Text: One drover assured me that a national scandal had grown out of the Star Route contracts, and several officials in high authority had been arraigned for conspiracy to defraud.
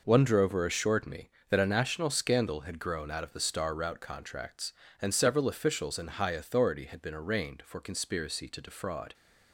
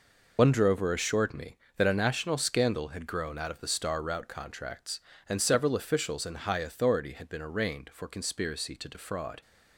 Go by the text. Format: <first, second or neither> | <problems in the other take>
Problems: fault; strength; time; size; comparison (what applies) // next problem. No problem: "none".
first | loses the start of "One"; at 0.3 s; 60 ms